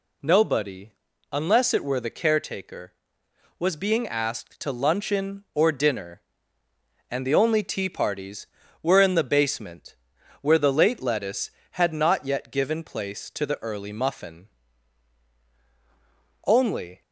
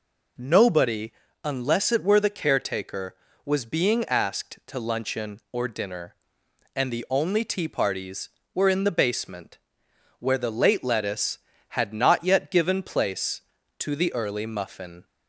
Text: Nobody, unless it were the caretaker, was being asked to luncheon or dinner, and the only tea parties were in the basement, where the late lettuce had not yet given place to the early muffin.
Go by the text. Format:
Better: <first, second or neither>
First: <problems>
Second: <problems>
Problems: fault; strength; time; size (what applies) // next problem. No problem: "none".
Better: second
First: goes on to say "Only"; from 16.4 s on; 0.54 s long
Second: none